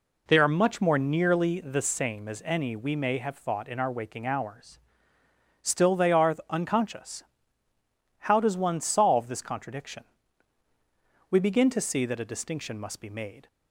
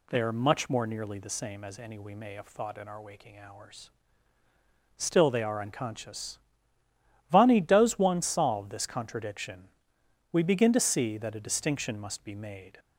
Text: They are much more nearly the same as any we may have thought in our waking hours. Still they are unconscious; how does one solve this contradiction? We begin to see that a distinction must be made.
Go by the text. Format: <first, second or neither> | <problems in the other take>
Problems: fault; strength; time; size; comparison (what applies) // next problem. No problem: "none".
first | says "vani" for "how"; at 7.3 s